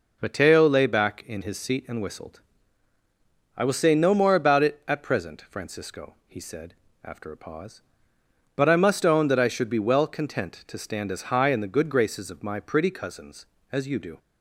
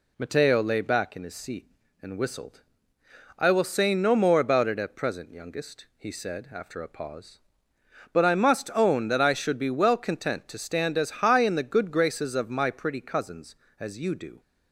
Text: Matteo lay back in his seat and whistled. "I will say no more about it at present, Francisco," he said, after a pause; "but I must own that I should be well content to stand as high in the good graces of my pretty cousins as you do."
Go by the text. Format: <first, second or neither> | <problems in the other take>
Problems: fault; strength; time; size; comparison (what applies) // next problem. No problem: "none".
first | says "Youngest" for "Francisco"; at 5.3 s